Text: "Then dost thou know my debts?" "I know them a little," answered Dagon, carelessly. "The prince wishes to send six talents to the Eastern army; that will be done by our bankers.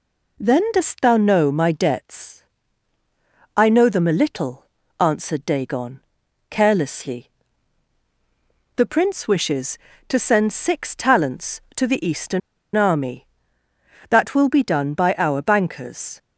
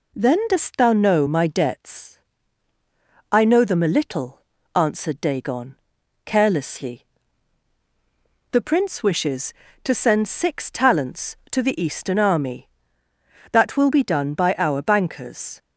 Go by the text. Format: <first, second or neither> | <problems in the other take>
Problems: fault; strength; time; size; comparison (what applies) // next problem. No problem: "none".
second | pauses between "Eastern" and "army"; slight; at 12.4 s; 0.35 s long